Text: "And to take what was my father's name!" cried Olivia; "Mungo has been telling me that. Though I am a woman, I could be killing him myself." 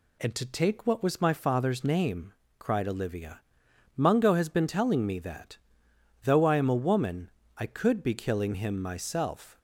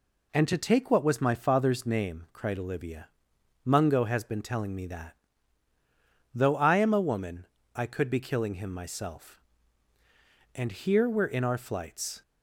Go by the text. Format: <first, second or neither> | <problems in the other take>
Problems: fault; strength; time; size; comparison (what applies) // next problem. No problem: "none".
first | goes on to say "And here we're in our flights"; strong; from 10.5 s on; 1.6 s long